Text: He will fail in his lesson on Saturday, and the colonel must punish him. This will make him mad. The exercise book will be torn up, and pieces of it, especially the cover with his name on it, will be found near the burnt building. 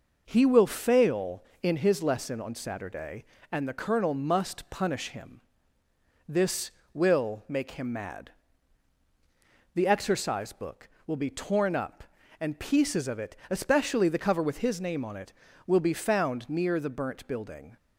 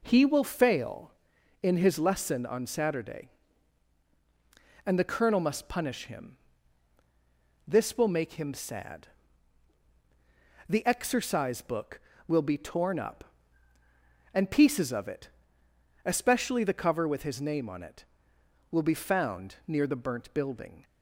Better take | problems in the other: first | says "sad" for "mad"; at 8.5 s

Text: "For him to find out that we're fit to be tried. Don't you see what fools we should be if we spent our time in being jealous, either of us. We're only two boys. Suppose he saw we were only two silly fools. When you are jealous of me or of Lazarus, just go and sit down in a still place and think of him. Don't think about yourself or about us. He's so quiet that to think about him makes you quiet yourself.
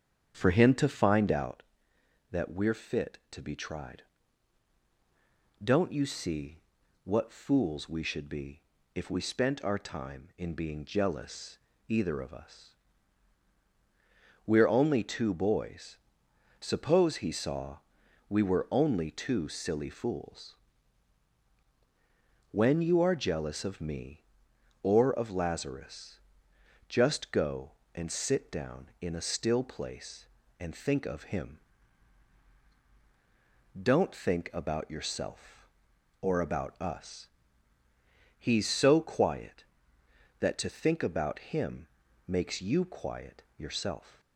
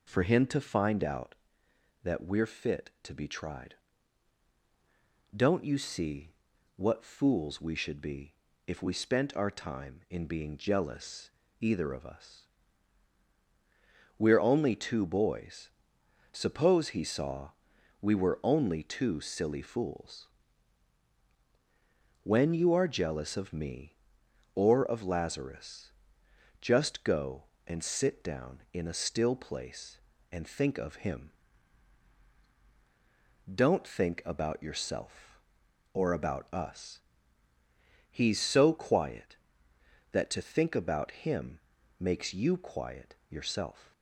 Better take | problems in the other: second | starts louder than the rest; strong; until 1.5 s; 8.5 dB // pauses between "see" and "what"; at 6.5 s; 0.44 s long; also in the second // pauses between "be" and "if"; slight; at 8.6 s; 0.32 s long; slight in the second // pauses between "saw" and "we"; noticeable; at 17.7 s; 0.50 s long; noticeable in the second // pauses between "him" and "makes"; at 41.8 s; 0.40 s long; also in the second

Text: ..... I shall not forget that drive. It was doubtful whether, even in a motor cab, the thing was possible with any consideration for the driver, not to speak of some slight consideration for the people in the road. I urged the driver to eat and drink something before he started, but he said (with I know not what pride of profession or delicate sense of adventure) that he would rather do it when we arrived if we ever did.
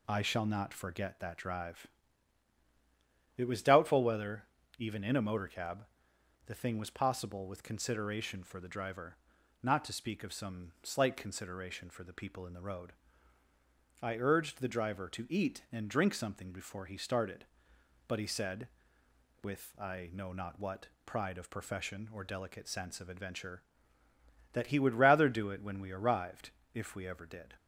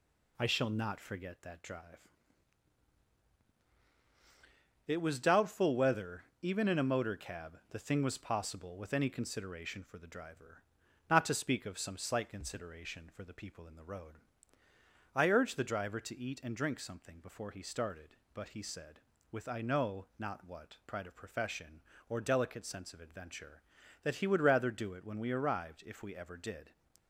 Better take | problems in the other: second | skips "any"; at 7.6 s // pauses between "what" and "pride"; slight; at 20.8 s; 0.18 s long // pauses between "arrived" and "if"; slight; at 26.5 s; 0.24 s long

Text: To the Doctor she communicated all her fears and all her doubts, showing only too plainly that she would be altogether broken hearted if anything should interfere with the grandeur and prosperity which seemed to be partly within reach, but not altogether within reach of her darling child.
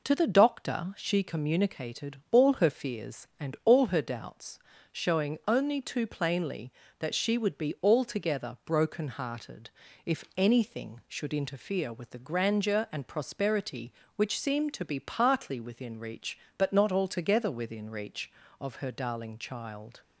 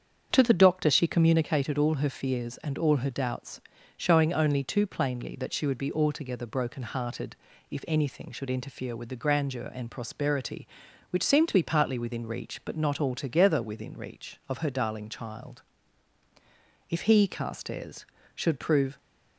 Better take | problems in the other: first | starts louder than the rest; strong; until 1.3 s; 7.5 dB // pauses between "hearted" and "if"; slight; at 7.3 s; 0.34 s long; also in the first // goes on to say "If he Carstairs should prove"; strong; from 16.8 s on; 2.0 s long

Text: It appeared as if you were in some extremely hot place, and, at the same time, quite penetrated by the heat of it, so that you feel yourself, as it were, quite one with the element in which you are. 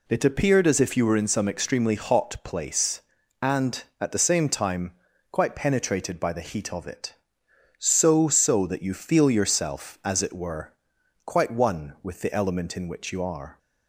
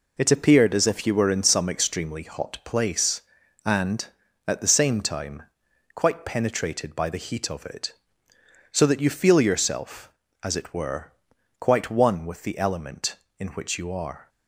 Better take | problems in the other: second | says "so" twice; at 8.2 s

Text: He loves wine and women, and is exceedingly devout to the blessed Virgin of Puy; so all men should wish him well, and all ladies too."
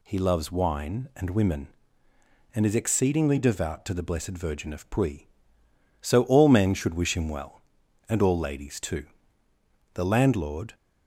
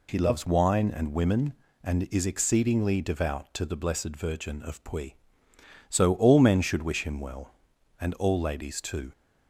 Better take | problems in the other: second | goes on to say "The landlord"; noticeable; from 9.9 s on; 0.80 s long

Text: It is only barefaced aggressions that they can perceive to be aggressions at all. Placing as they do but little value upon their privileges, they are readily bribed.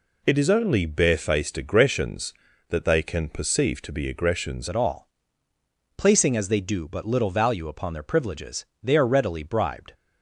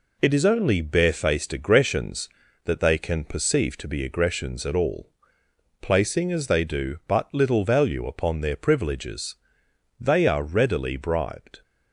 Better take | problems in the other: second | changes voice at "at"; from 4.6 s on; 5.3 s long

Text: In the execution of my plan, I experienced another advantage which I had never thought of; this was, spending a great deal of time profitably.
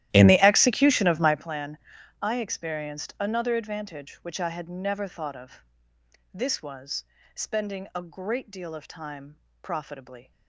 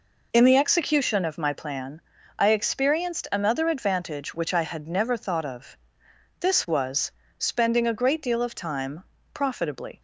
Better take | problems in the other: second | starts louder than the rest; strong; until 1.5 s; 13.5 dB // pauses between "time" and "profitably"; slight; at 9.3 s; 0.22 s long; slight in the second

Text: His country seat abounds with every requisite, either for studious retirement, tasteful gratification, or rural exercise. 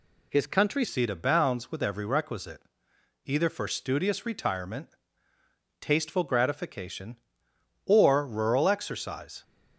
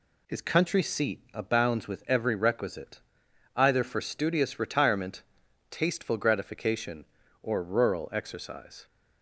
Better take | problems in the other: second | changes voice at "seat"; from 0.8 s on; 8.6 s long

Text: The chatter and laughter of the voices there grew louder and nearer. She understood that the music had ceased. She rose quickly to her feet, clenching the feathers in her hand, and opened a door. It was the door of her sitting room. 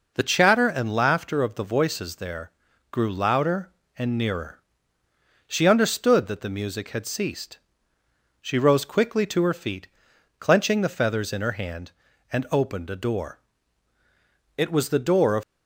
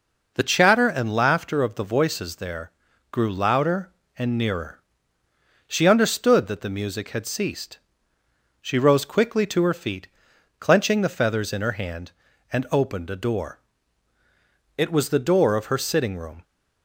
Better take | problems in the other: second | pauses between "there" and "grew"; at 2.5 s; 0.40 s long; also in the second // stops before "her sitting room"; at 15.4 s

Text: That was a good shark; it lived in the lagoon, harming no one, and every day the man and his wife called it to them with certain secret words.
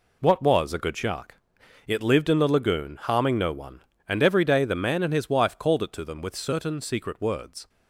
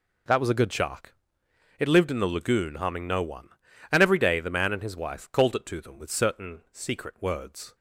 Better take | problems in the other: second | says "What" for "That"; at 0.2 s

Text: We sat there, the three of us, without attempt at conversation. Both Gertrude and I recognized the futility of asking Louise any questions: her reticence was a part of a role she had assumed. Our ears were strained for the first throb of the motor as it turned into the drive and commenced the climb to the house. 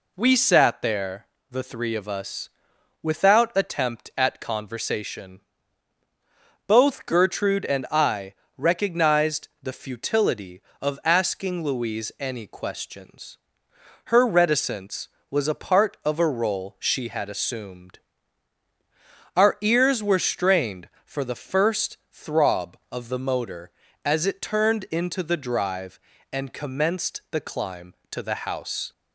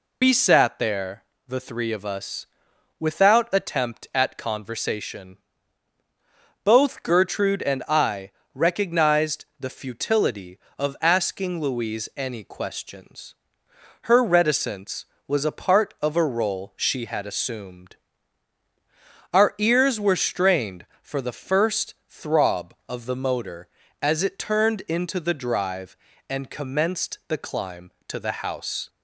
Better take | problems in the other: first | loses the start of "We"; at 0.2 s; 90 ms // pauses between "I" and "recognized"; slight; at 8.3 s; 0.24 s long; slight in the first // pauses between "first" and "throb"; slight; at 21.9 s; 0.16 s long; slight in the first

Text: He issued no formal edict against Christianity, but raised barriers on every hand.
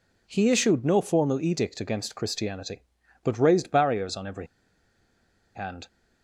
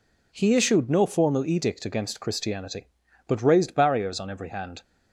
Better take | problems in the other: second | pauses between "every" and "hand"; at 4.4 s; 1.0 s long

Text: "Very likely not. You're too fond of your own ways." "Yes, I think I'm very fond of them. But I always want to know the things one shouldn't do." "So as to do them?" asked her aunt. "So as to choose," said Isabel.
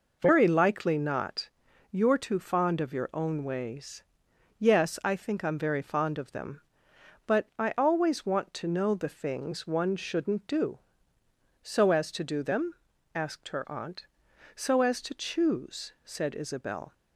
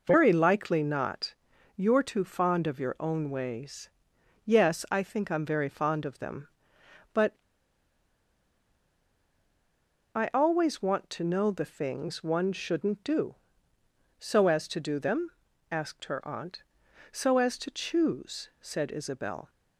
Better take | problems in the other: first | pauses between "But" and "I"; strong; at 7.3 s; 2.7 s long

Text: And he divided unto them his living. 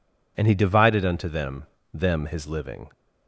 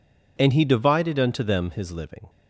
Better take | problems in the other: second | says "them" twice; at 1.9 s

